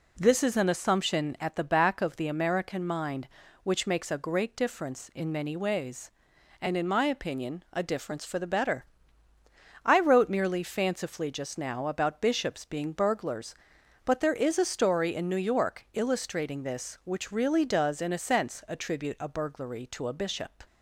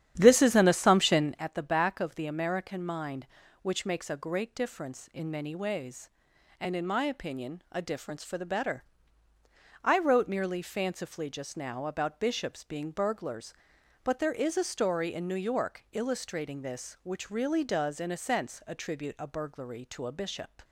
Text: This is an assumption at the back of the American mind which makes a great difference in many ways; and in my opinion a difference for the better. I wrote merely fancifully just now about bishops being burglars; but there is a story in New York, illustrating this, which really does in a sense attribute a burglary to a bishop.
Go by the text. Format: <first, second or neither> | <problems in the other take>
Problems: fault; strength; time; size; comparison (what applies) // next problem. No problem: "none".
first | starts louder than the rest; strong; until 1.4 s; 10 dB